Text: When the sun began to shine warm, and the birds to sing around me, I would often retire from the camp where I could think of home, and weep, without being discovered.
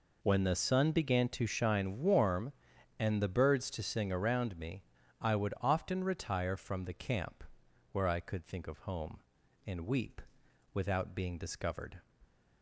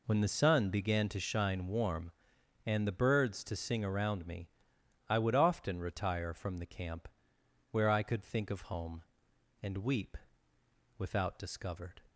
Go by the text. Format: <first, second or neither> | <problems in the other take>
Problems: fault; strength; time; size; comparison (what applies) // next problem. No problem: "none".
first | pauses between "camp" and "where"; noticeable; at 7.0 s; 0.64 s long; noticeable in the first // skips "being"; at 11.3 s